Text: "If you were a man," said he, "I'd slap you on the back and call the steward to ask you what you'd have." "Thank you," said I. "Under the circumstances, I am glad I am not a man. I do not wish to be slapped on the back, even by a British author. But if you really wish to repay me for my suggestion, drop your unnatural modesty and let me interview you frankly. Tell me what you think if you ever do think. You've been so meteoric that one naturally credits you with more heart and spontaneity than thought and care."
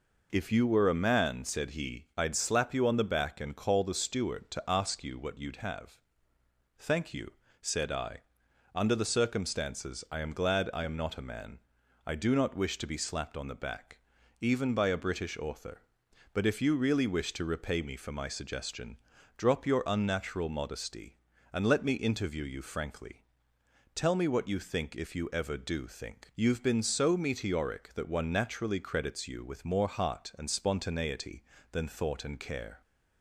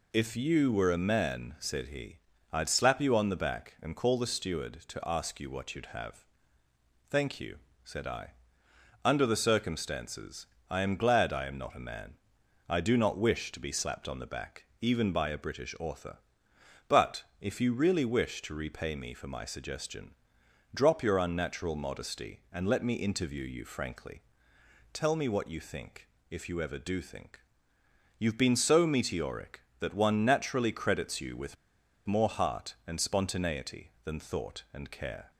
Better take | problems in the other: first | pauses between "think" and "if"; slight; at 26.0 s; 0.22 s long // pauses between "with" and "more"; noticeable; at 31.5 s; 0.50 s long

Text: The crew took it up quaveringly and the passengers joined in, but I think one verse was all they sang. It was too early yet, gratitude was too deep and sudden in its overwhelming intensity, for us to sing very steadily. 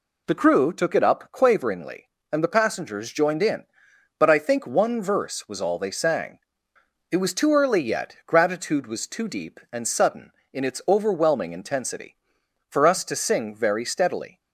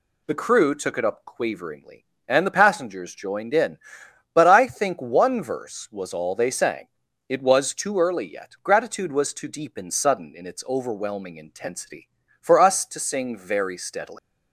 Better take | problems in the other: first | leaves "steadily" unfinished; at 14.1 s; 150 ms

